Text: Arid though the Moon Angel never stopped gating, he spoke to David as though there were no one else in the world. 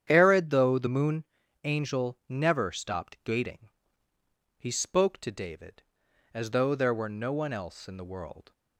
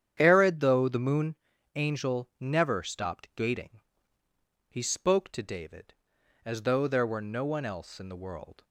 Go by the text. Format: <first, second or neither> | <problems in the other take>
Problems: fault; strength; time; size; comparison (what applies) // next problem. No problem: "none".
neither | starts louder than the rest; strong; the same in both // pauses between "Moon" and "Angel"; the same in both